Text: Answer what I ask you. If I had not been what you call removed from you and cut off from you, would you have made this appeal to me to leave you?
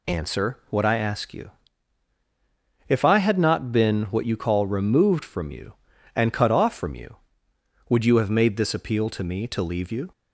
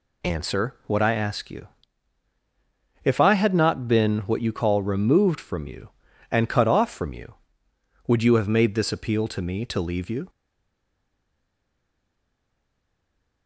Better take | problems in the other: first | stays silent after the last word; strong; from 10.2 s on; 3.2 s long

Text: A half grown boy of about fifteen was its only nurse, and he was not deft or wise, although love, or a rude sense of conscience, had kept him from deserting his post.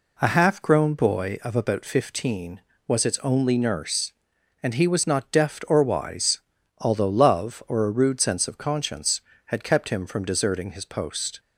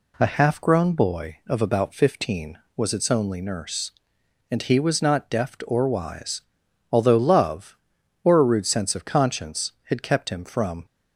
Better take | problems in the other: first | stops before "deserting his post"; at 10.8 s

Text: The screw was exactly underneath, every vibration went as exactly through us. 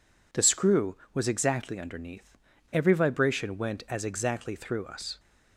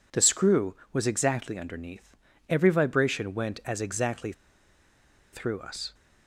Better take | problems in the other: first | pauses between "exactly" and "through"; at 4.3 s; 1.0 s long

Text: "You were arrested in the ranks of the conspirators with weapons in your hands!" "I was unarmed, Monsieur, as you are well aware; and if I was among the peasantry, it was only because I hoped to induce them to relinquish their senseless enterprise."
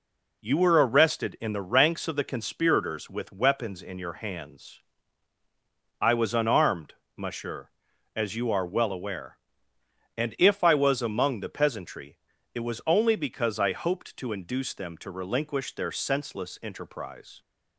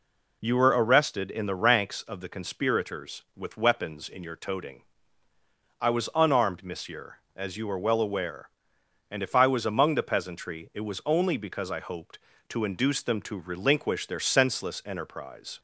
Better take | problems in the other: first | says "toting" for "hands"; at 4.3 s

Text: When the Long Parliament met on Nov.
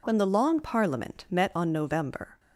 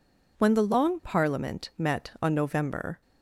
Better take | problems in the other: neither | none

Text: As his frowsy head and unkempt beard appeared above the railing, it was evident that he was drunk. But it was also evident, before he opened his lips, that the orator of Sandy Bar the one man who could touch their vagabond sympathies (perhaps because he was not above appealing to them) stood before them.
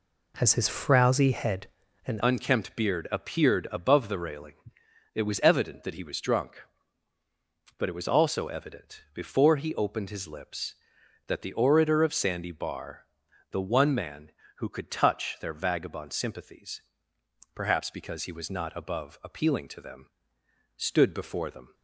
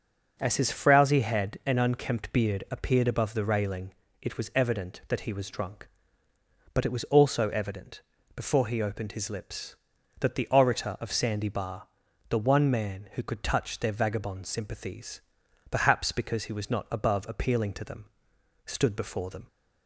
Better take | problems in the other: second | changes voice at "unkempt"; from 2.2 s on; 19.5 s long // pauses between "Bar" and "the"; noticeable; at 13.0 s; 0.46 s long; also in the second

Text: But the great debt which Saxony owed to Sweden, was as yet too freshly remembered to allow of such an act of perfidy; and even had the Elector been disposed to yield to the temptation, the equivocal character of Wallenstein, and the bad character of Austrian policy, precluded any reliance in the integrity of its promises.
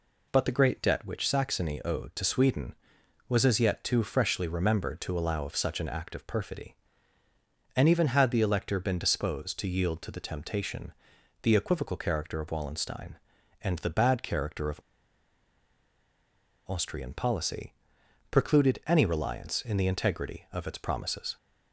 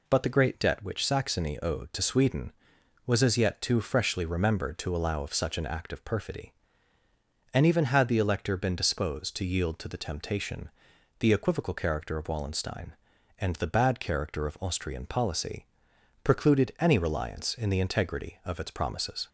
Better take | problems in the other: second | pauses between "of" and "Austrian"; strong; at 14.7 s; 1.8 s long

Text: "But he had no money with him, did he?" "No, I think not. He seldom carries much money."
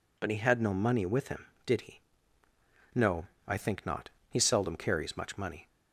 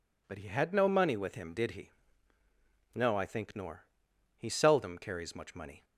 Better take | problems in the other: first | says "nor" for "not"; at 3.5 s

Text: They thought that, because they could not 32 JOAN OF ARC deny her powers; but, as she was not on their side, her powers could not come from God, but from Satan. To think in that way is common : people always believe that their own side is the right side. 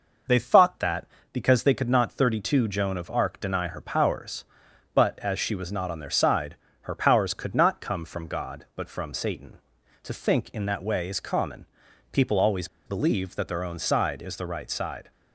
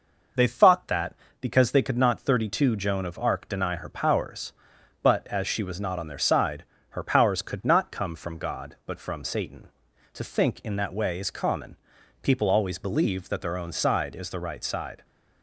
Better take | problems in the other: second | pauses between "always" and "believe"; slight; at 12.6 s; 0.20 s long

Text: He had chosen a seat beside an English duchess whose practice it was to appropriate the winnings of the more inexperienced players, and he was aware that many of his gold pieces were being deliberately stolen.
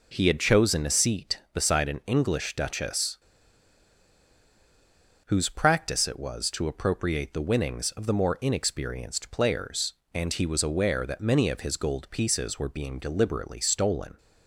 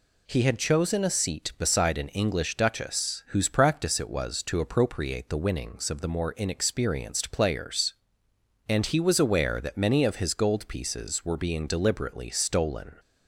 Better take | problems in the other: second | pauses between "duchess" and "whose"; strong; at 3.1 s; 2.1 s long

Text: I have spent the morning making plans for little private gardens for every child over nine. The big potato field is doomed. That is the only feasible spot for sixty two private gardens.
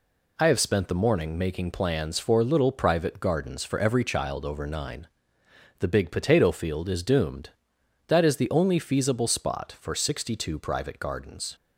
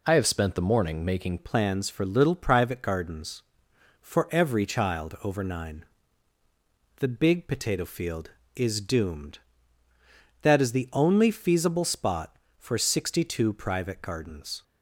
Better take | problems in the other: first | changes voice at "plans"; from 1.3 s on; 13.3 s long

